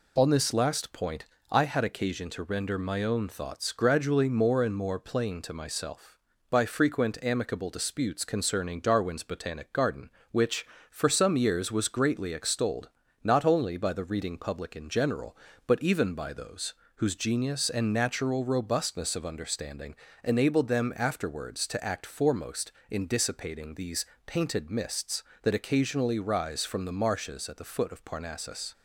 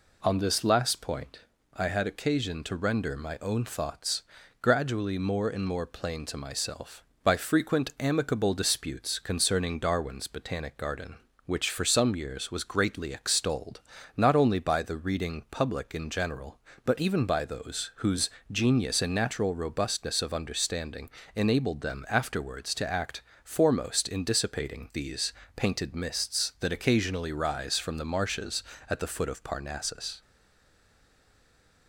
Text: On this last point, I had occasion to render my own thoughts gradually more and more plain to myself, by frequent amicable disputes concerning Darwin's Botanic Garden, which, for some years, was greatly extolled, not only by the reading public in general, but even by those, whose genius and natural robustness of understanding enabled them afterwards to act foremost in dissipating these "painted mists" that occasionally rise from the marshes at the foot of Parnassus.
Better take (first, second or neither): first